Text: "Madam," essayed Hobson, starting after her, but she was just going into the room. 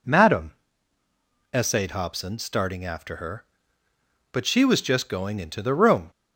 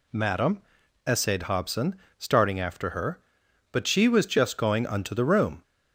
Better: first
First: none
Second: says "unto" for "into"; at 4.8 s

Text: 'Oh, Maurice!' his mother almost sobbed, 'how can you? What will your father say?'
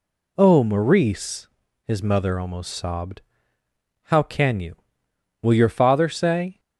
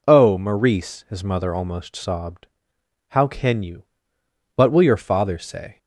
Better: second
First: skips "What"; at 5.0 s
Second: none

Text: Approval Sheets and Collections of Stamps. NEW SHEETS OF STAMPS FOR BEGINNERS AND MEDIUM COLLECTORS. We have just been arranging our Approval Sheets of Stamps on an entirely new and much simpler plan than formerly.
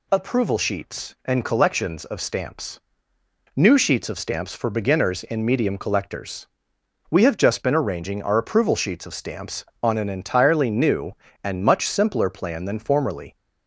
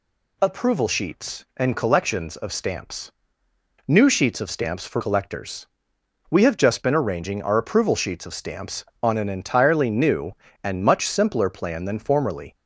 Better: first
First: none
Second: skips "BEGINNERS AND MEDIUM"; at 5.0 s

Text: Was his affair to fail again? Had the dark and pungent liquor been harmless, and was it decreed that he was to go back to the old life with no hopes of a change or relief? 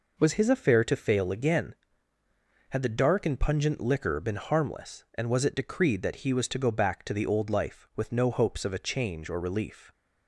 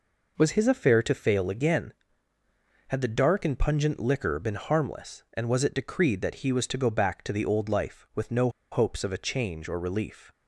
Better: first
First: none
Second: pauses between "no" and "hopes"; slight; at 8.4 s; 0.22 s long

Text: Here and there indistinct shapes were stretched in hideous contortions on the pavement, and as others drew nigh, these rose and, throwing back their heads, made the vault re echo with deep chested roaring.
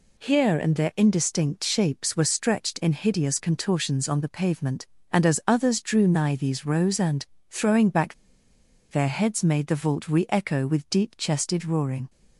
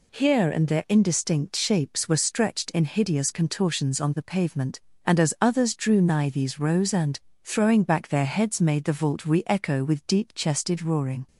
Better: second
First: pauses between "back" and "their"; noticeable; at 8.1 s; 0.77 s long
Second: none

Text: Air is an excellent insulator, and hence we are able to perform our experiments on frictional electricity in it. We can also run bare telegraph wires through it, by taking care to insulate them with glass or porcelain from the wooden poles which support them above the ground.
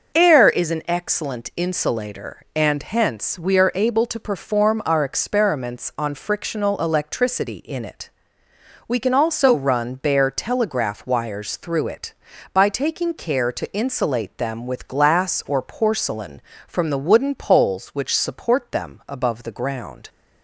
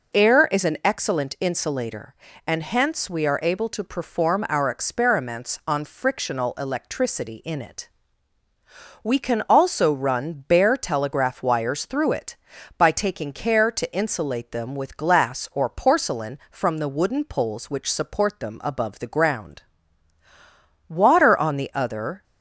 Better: first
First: none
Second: goes on to say "Water on the other"; noticeable; from 20.9 s on; 1.2 s long

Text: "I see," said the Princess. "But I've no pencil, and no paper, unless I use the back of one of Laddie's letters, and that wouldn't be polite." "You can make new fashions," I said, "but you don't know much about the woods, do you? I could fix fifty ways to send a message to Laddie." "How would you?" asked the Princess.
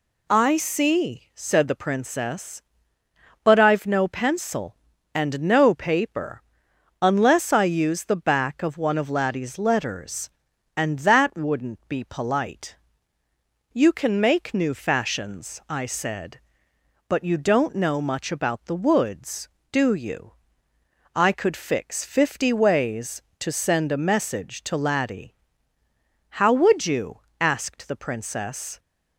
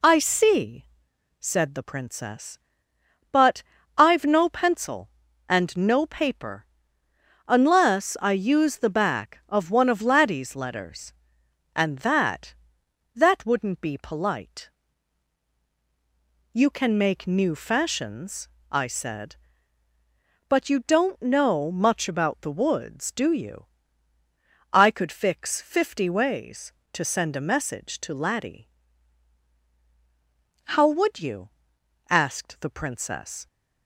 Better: first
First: none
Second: pauses between "But" and "I've"; slight; at 3.6 s; 0.32 s long // says "that" twice; at 13.1 s

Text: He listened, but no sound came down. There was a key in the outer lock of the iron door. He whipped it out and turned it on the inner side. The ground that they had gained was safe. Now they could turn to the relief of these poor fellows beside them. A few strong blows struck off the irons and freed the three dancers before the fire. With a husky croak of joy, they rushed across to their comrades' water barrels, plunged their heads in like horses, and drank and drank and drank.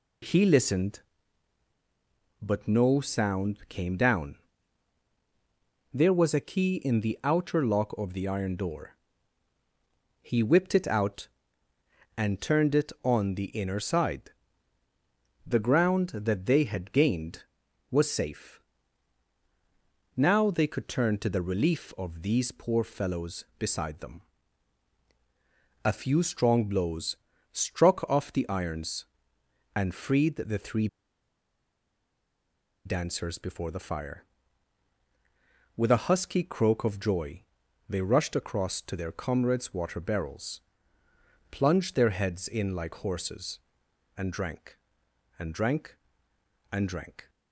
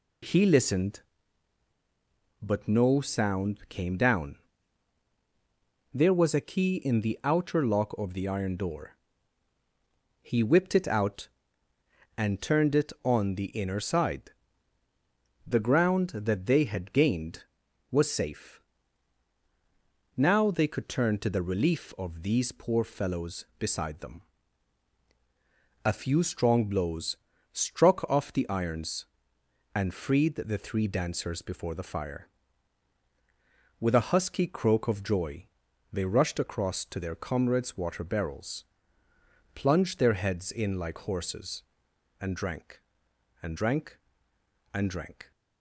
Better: second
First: pauses between "blows" and "struck"; slight; at 27.1 s; 0.34 s long // pauses between "three" and "dancers"; strong; at 30.8 s; 1.9 s long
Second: pauses between "blows" and "struck"; slight; at 27.1 s; 0.34 s long

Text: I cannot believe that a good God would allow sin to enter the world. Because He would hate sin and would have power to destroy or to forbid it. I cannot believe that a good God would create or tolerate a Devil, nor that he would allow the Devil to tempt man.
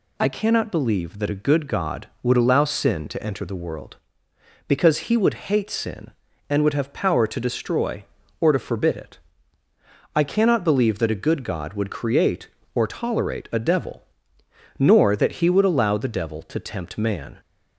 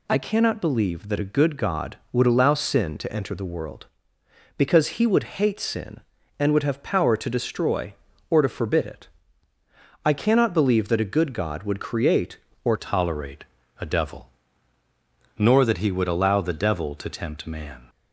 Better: first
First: none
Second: changes voice at "tolerate"; from 12.7 s on; 5.1 s long // pauses between "tolerate" and "a"; at 13.4 s; 0.38 s long

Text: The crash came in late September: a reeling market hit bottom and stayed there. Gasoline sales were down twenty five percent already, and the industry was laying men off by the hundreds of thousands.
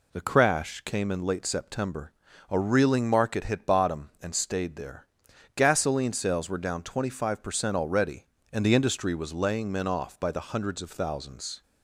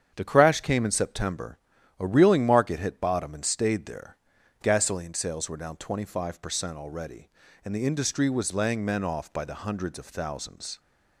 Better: first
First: none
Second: starts louder than the rest; strong; until 1.1 s; 8 dB // skips "late"; at 0.9 s

